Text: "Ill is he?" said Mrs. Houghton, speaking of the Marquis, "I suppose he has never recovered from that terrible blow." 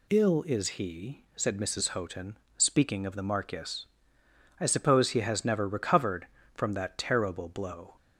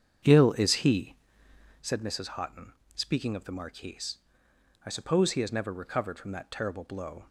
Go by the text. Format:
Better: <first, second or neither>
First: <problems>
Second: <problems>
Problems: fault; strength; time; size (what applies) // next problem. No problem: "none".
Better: first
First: none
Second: starts louder than the rest; strong; until 1.9 s; 7.5 dB